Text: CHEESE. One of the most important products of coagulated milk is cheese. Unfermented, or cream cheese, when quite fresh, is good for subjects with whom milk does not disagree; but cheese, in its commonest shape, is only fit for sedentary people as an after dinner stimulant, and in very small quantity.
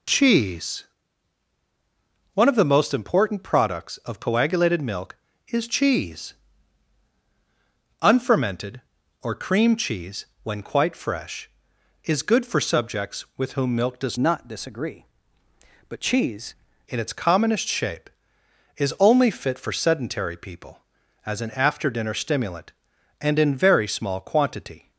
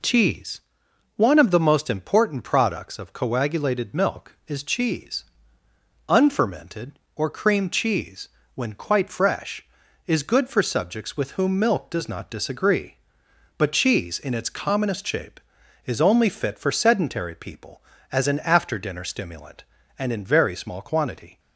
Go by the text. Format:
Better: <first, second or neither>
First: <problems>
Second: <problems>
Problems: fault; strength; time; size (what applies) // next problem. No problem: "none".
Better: second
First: changes voice from "not" to "cheese"; from 14.1 to 16.5 s; 2.4 s long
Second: none